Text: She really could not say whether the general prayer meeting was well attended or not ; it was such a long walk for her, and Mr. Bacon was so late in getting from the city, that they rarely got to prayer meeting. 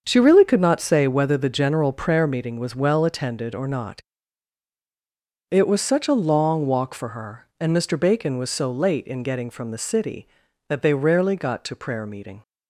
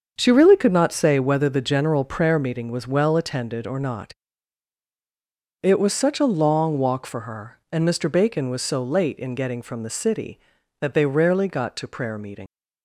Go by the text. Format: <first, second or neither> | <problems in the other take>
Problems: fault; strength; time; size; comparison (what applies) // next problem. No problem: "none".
first | starts louder than the rest; until 1.1 s; 7 dB; also in the first // leaves "meeting" unfinished; at 12.4 s; 75 ms